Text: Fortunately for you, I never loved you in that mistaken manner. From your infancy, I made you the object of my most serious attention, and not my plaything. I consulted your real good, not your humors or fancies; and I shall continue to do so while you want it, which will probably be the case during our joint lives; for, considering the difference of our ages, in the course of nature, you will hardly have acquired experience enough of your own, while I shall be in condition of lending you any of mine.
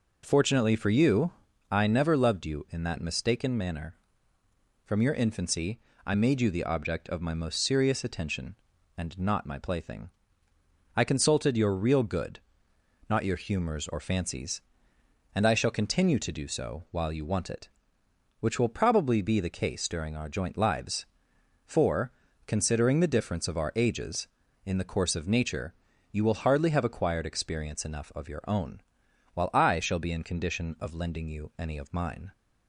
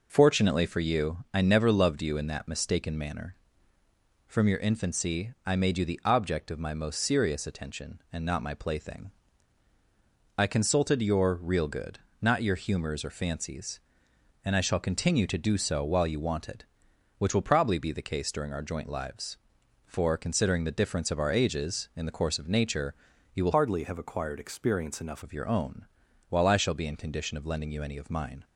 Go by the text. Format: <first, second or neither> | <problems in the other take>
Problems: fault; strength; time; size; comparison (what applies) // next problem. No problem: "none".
first | changes voice from "hardly" to "enough"; from 23.5 to 25.2 s; 1.7 s long